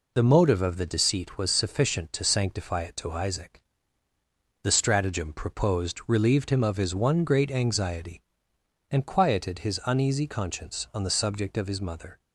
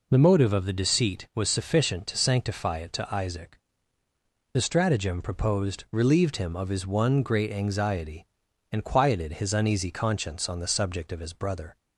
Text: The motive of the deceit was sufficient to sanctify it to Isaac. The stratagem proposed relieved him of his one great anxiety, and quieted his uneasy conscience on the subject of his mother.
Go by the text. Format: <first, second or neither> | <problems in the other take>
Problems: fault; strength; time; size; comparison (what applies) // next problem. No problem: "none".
first | says "brother" for "mother"; at 11.3 s